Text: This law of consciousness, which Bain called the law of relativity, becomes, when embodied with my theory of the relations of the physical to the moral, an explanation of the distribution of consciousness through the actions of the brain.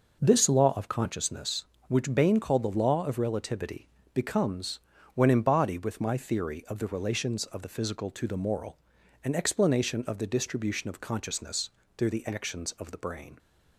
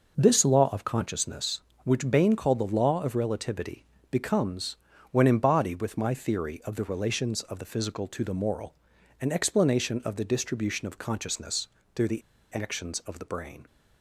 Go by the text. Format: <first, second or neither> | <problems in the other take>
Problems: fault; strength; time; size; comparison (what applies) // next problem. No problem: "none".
first | starts louder than the rest; noticeable; until 1.2 s; 6 dB; noticeable in the first // pauses between "consciousness" and "through"; slight; at 11.6 s; 0.26 s long; slight in the first // pauses between "the" and "actions"; slight; at 12.2 s; 0.31 s long